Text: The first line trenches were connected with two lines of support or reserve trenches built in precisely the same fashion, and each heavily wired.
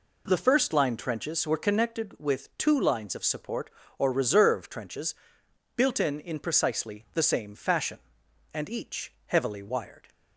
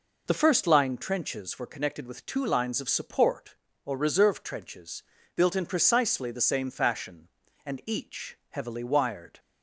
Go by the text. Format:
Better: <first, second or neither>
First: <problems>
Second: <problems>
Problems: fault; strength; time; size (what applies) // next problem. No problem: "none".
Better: second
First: pauses between "trenches" and "built"; noticeable; at 5.1 s; 0.62 s long // says "in" twice; at 6.1 s // pauses between "each" and "heavily"; slight; at 9.1 s; 0.16 s long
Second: pauses between "trenches" and "built"; slight; at 5.0 s; 0.36 s long